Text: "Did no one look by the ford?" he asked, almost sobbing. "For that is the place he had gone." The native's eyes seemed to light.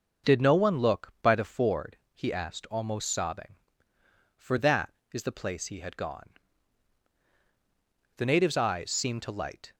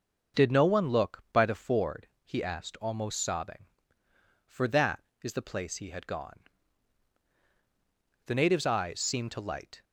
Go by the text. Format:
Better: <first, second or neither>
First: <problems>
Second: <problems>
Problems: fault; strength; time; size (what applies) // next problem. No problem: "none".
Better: neither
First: starts louder than the rest; noticeable; until 1.3 s; 6 dB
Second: starts louder than the rest; noticeable; until 1.4 s; 6 dB